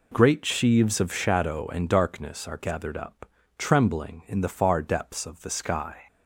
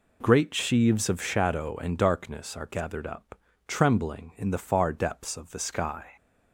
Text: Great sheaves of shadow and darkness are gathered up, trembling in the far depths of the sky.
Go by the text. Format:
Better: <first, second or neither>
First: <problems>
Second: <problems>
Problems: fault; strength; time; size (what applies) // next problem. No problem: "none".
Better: neither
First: none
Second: none